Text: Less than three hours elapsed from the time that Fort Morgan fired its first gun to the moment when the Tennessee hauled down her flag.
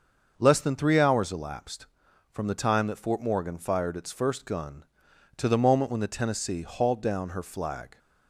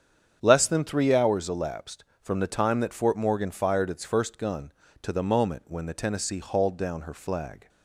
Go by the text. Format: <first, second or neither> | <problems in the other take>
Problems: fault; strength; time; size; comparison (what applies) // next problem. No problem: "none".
neither | starts louder than the rest; the same in both